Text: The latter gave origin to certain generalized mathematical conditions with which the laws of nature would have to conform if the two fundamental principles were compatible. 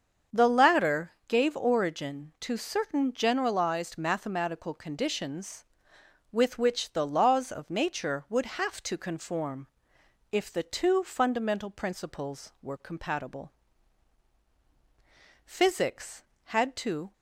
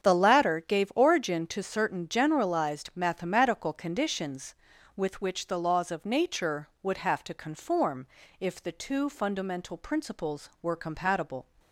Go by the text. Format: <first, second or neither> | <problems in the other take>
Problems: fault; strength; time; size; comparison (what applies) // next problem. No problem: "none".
second | starts louder than the rest; until 1.4 s; 7 dB; strong in the second // pauses between "latter" and "gave"; slight; at 1.1 s; 0.16 s long // pauses between "conform" and "if"; noticeable; at 9.6 s; 0.64 s long; slight in the second // goes on to say "Physics had to"; strong; from 15.4 s on; 1.6 s long